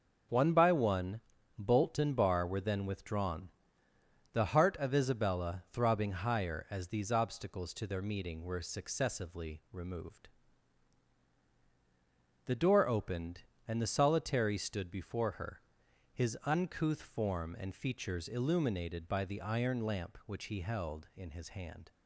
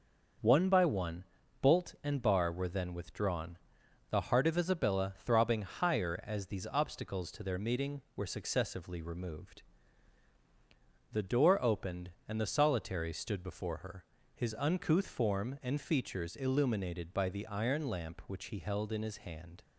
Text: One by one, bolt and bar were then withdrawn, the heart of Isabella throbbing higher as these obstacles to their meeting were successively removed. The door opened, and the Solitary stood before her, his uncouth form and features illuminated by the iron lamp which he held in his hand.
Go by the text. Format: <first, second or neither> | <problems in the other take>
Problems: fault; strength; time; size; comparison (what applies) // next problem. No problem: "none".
neither | none